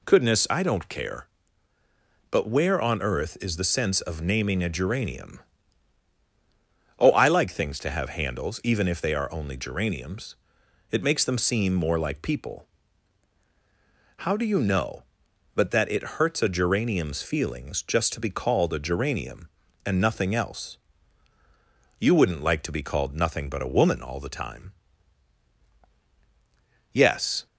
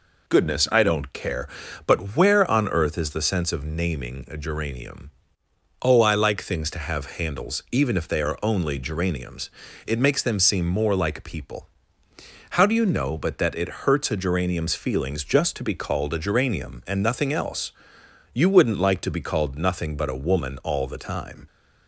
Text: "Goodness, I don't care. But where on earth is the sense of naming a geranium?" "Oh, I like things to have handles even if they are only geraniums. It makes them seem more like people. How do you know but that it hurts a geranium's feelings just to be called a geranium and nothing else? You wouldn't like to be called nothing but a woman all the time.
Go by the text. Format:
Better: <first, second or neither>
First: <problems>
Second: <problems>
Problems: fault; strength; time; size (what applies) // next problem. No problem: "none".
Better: second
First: goes on to say "Yes"; from 26.9 s on; 0.54 s long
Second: none